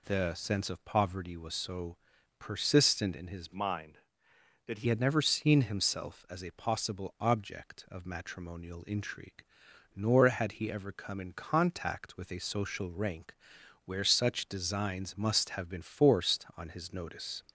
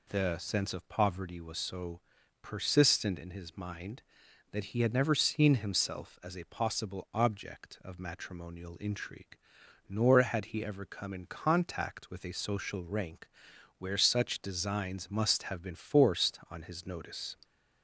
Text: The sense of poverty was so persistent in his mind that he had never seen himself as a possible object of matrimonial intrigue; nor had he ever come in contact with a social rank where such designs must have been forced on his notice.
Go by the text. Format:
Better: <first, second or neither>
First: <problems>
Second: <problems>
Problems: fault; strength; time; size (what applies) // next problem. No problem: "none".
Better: second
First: pauses between "so" and "persistent"; at 1.9 s; 0.42 s long // changes voice from "mind" to "he"; from 3.5 to 4.8 s; 1.3 s long // pauses between "rank" and "where"; noticeable; at 13.3 s; 0.52 s long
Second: pauses between "so" and "persistent"; at 2.0 s; 0.41 s long // pauses between "rank" and "where"; noticeable; at 13.2 s; 0.52 s long